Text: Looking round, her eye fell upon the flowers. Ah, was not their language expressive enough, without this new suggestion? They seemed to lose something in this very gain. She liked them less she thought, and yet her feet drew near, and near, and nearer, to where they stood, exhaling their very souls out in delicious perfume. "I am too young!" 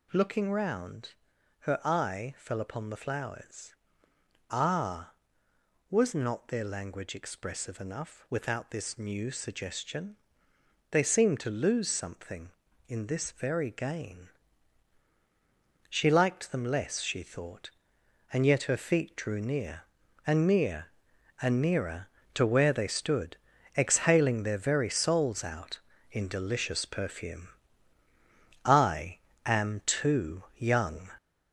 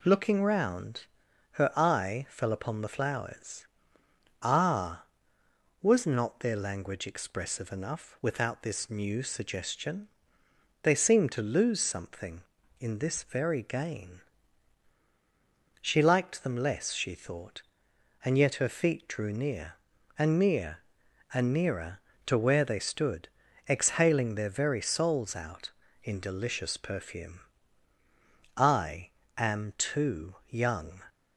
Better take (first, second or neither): second